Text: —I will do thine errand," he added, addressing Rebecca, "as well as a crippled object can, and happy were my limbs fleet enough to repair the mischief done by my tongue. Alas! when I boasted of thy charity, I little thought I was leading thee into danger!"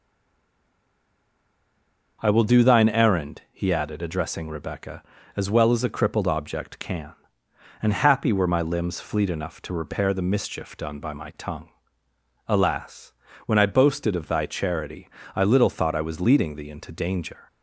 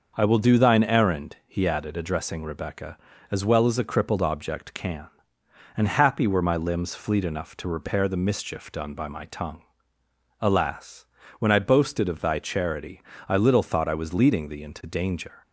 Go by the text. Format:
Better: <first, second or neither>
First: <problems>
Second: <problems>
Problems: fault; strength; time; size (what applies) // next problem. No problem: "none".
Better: second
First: stays silent before the first word; until 2.2 s; 2.2 s long // starts louder than the rest; until 3.2 s; 6 dB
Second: starts louder than the rest; until 1.1 s; 6.5 dB